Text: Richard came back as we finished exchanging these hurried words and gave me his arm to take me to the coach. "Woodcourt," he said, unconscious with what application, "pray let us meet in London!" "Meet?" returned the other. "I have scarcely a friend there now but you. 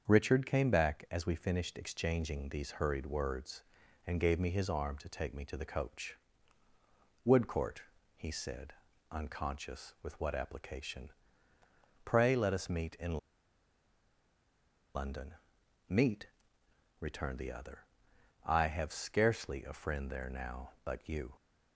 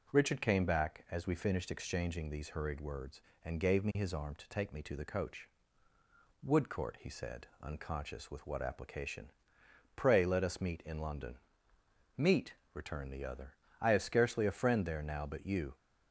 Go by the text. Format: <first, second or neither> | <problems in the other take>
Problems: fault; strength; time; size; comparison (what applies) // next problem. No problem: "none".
second | starts louder than the rest; until 1.1 s; 7 dB // pauses between "in" and "London"; strong; at 13.1 s; 1.7 s long